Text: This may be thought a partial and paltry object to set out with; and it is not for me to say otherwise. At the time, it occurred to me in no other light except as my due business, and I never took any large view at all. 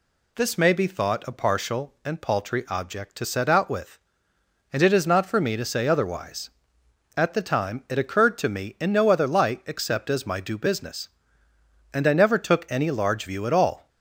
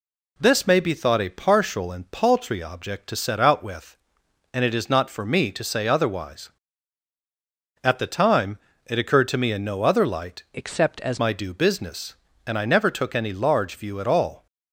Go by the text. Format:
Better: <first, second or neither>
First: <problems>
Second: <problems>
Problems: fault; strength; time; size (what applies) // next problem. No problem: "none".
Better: first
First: none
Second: changes voice from "except" to "as"; from 10.5 to 11.1 s; 0.6 s long